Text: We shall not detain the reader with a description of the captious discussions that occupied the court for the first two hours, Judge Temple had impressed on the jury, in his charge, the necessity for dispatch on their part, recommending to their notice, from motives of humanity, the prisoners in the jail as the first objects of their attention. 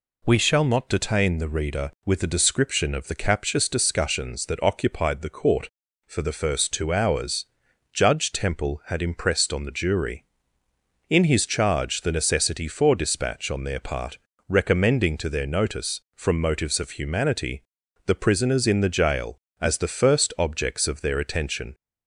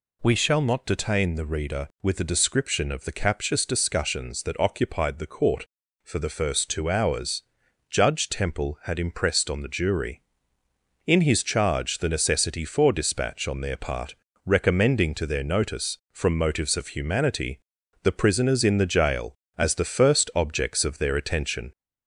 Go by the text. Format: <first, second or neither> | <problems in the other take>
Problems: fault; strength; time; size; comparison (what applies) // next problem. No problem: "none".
first | gets louder; slight; throughout; 2 dB